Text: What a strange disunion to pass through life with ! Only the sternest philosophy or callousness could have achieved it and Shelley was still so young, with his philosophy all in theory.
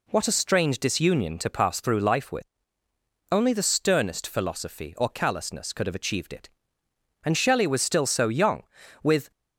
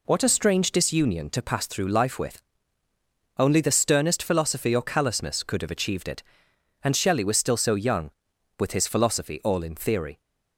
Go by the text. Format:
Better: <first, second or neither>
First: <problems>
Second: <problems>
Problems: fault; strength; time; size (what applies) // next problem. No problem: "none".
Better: second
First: stops before "his philosophy all in theory"; at 9.3 s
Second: none